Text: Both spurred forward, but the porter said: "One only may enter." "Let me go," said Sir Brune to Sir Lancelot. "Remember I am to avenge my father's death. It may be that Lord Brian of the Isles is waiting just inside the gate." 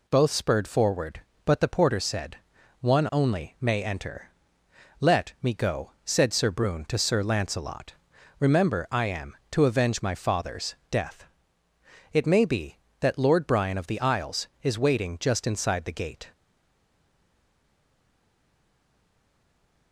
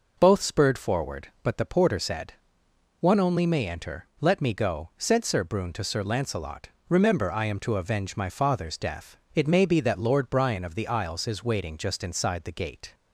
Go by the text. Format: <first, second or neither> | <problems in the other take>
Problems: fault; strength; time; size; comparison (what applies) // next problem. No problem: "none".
second | pauses between "father's" and "death"; slight; at 10.7 s; 0.16 s long // stays silent after the last word; strong; from 16.3 s on; 3.6 s long